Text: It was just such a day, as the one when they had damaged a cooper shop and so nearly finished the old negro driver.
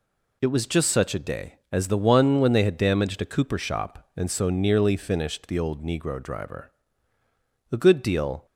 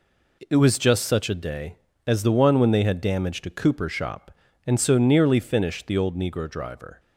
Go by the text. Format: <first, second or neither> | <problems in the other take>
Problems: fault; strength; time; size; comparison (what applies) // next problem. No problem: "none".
second | goes on to say "A good deal"; noticeable; from 7.7 s on; 0.74 s long